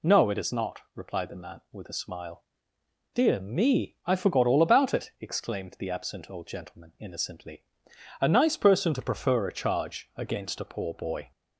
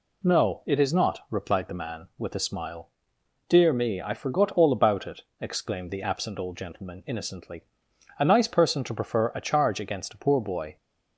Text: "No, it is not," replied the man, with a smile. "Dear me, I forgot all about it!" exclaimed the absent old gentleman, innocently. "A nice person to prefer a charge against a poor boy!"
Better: neither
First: none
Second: none

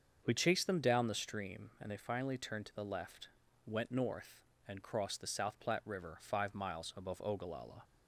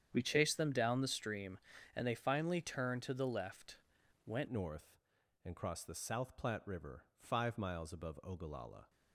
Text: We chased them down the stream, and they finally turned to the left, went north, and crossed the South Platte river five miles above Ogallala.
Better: first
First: starts louder than the rest; until 1.2 s; 6.5 dB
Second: starts louder than the rest; strong; until 1.1 s; 8.5 dB // changes voice at "north"; from 4.4 s on; 4.4 s long

